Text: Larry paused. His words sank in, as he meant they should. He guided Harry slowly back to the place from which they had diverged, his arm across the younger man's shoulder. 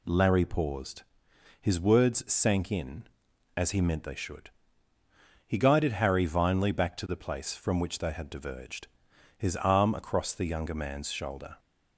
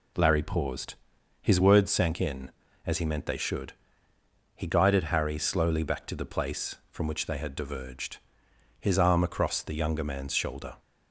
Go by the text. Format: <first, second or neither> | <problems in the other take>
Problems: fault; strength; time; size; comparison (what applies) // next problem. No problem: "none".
second | says "vinely" for "slowly"; at 6.2 s